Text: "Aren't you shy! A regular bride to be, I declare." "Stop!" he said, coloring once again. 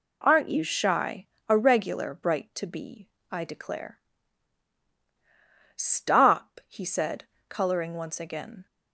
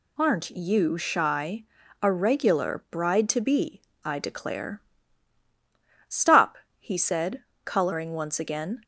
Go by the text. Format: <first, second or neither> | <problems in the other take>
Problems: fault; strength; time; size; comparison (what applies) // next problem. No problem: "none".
second | says "bright" for "bride"; at 2.1 s